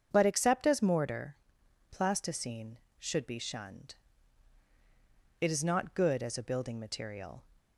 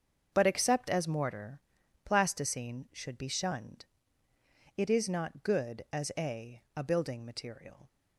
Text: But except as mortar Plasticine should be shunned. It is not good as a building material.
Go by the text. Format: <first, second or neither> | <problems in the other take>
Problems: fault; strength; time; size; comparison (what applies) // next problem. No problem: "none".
first | starts louder than the rest; until 1.3 s; 7 dB; also in the first // pauses between "mortar" and "Plasticine"; noticeable; at 1.5 s; 0.46 s long; noticeable in the first // says "a" twice; at 6.7 s